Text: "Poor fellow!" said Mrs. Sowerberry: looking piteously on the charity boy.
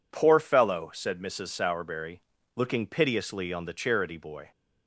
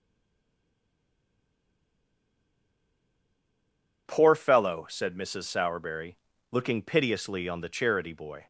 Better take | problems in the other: first | stays silent before the first word; strong; until 4.0 s; 4.0 s long

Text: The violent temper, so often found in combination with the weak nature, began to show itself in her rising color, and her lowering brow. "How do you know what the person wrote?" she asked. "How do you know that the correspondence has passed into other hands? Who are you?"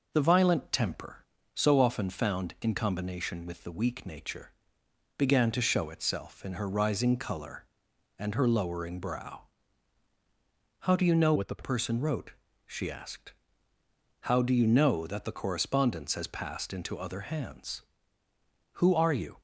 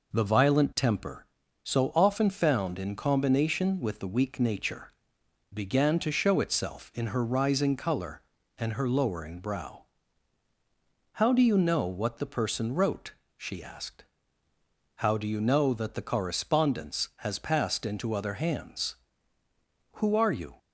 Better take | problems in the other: second | changes voice from "what" to "the"; from 11.3 to 11.6 s; 0.3 s long

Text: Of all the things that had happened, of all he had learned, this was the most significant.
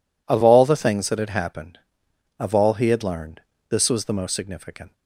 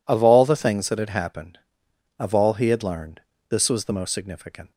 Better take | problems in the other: neither | none

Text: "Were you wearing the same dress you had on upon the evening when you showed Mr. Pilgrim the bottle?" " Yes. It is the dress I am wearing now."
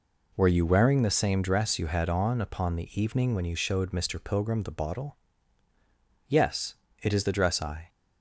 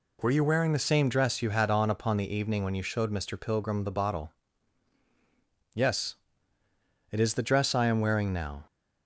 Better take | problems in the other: second | stops before "am wearing now"; at 7.8 s

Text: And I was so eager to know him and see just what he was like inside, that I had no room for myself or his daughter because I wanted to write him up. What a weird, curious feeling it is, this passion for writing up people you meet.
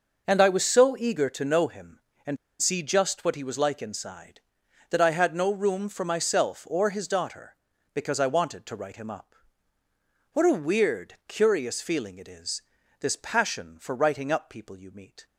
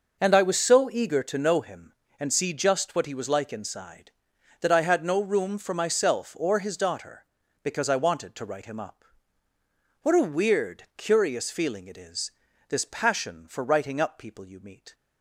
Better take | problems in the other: second | pauses between "and" and "see"; slight; at 2.3 s; 0.24 s long

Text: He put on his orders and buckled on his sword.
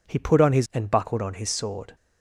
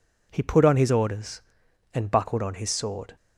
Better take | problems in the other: second | skips "orders"; at 0.6 s

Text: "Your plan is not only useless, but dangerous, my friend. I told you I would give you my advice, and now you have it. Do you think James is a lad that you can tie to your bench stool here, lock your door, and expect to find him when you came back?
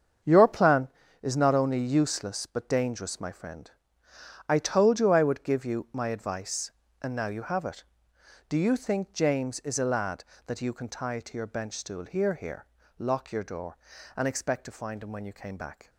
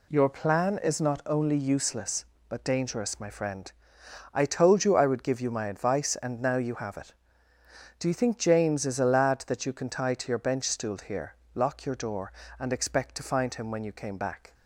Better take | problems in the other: second | starts louder than the rest; strong; until 1.5 s; 7.5 dB // says "here" twice; at 12.3 s

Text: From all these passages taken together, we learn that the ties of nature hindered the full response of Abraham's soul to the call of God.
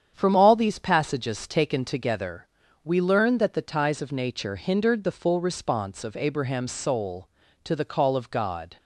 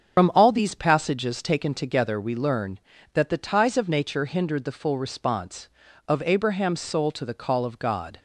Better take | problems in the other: first | loses the start of "From"; at 0.1 s; 95 ms // starts louder than the rest; strong; until 1.2 s; 7 dB; strong in the first

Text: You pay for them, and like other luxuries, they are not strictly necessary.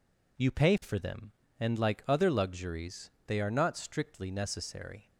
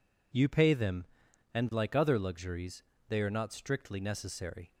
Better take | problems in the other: first | skips "for"; at 0.7 s

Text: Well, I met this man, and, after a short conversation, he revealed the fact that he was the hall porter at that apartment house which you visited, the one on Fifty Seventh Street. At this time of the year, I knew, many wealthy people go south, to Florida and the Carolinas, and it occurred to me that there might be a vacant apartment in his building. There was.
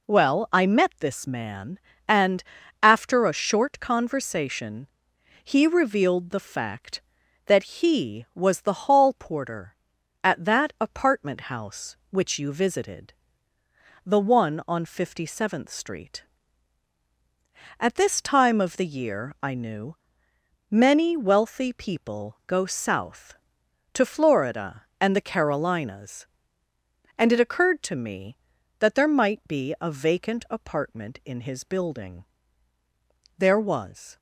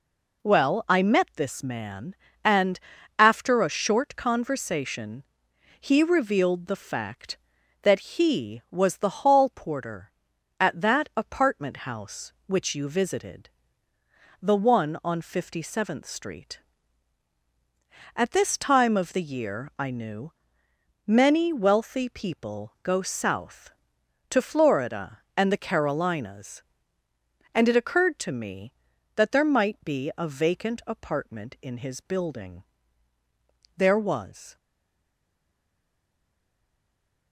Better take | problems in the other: first | stays silent after the last word; strong; from 34.5 s on; 2.8 s long

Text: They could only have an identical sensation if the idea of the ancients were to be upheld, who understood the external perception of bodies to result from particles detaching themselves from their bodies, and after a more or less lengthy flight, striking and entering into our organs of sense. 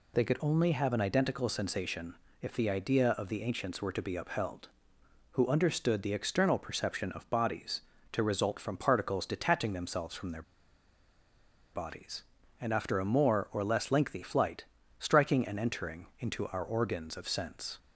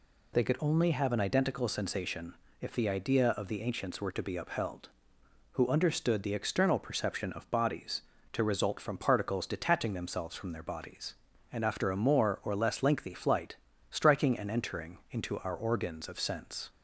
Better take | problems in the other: second | pauses between "sensation" and "if"; slight; at 2.1 s; 0.26 s long; slight in the second // pauses between "their" and "bodies"; strong; at 10.4 s; 1.3 s long

